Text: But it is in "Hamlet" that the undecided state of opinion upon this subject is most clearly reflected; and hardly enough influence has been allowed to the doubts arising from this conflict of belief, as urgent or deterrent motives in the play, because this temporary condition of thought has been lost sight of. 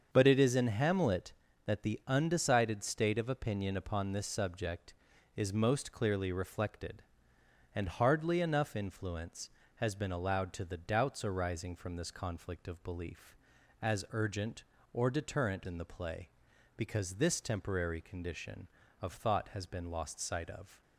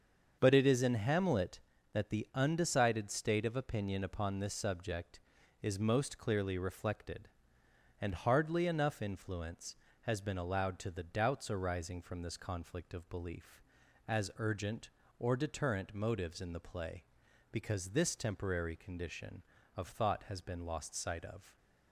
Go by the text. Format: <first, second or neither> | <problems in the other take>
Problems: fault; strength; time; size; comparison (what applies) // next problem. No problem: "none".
second | starts louder than the rest; until 1.1 s; 7 dB; also in the second // skips "motives"; at 15.6 s